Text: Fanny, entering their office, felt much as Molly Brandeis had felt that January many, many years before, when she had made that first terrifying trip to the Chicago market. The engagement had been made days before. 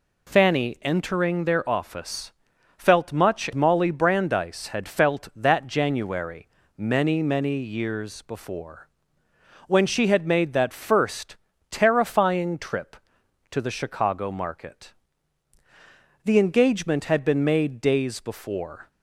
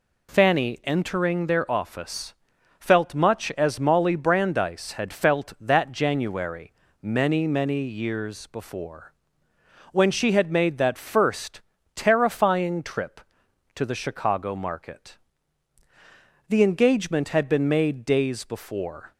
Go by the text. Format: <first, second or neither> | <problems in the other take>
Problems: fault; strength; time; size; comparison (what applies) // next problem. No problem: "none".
second | skips "as"; at 3.5 s // pauses between "January" and "many"; slight; at 6.4 s; 0.30 s long; slight in the second // pauses between "first" and "terrifying"; slight; at 11.3 s; 0.34 s long; slight in the second